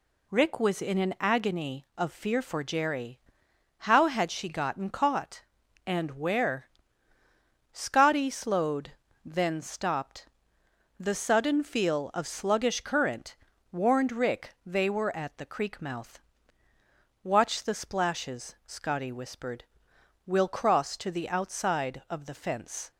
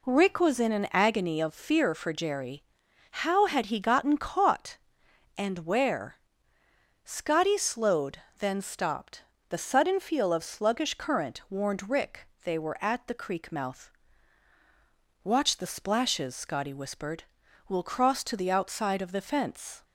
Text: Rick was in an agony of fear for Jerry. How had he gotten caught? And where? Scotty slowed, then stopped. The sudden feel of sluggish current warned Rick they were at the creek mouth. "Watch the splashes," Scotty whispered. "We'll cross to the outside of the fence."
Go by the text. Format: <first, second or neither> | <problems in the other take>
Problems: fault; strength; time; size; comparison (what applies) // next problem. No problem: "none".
second | says "she" for "he"; at 4.3 s // pauses between "current" and "warned"; slight; at 13.3 s; 0.36 s long // pauses between "Rick" and "they"; slight; at 14.5 s; 0.16 s long; slight in the second